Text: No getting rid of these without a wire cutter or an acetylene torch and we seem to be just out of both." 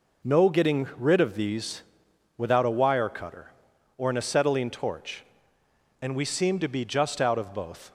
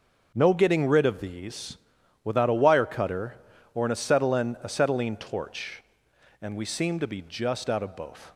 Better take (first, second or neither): first